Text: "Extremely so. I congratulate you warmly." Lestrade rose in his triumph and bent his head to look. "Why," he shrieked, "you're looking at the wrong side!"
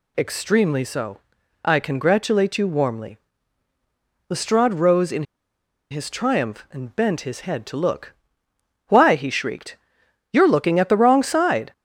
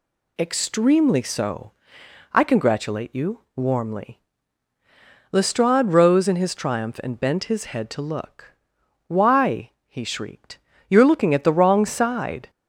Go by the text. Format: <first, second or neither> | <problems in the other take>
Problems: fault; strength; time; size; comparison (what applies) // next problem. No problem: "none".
second | pauses between "in" and "his"; noticeable; at 5.2 s; 0.68 s long